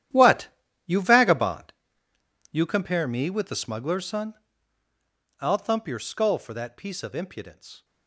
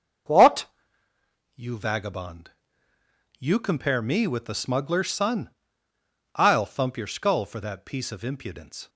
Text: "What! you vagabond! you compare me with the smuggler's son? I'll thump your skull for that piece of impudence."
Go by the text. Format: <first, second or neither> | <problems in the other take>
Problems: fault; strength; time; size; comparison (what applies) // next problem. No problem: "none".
second | gets quieter; strong; throughout; 15.5 dB // starts louder than the rest; strong; until 1.5 s; 11 dB; also in the second